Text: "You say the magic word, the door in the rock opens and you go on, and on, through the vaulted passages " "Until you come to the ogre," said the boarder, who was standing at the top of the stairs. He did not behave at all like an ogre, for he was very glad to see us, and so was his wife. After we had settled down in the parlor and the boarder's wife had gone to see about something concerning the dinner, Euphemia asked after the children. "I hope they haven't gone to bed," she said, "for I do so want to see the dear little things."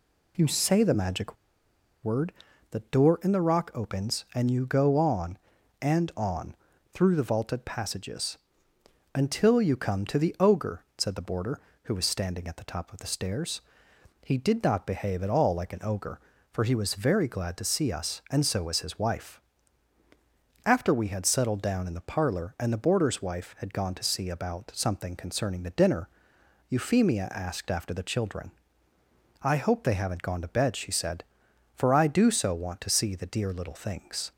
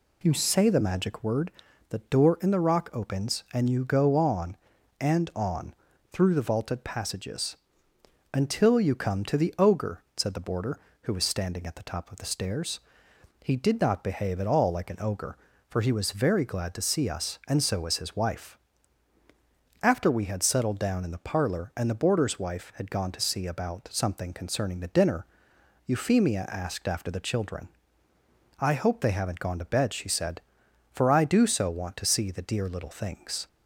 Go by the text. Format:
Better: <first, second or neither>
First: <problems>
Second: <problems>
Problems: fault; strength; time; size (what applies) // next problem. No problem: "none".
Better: second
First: pauses between "magic" and "word"; noticeable; at 1.3 s; 0.69 s long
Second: none